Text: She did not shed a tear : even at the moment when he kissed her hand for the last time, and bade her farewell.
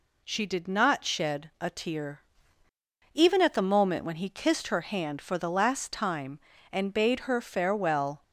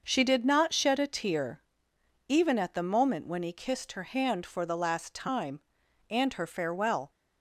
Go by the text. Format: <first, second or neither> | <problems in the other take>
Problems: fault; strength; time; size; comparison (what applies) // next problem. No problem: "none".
first | starts louder than the rest; until 1.0 s; 6 dB // skips "bade"; at 6.3 s